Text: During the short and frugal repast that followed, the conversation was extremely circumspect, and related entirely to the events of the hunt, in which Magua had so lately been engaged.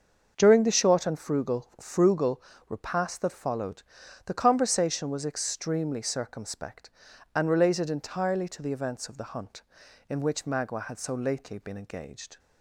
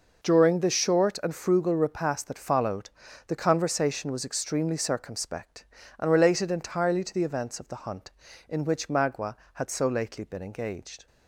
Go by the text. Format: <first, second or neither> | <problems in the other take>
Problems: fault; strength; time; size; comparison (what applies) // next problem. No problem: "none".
second | starts louder than the rest; until 1.3 s; 6.5 dB // says "frugal" twice; at 1.7 s